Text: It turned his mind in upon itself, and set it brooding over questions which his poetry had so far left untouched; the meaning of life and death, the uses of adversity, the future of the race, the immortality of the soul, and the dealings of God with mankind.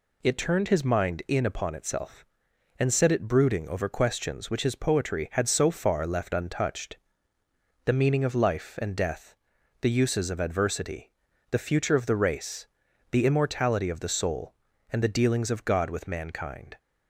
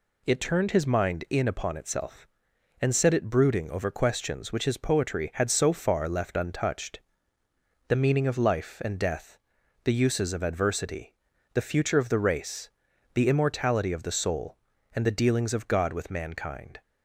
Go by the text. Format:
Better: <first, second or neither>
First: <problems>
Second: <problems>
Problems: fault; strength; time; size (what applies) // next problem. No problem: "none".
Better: neither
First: none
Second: none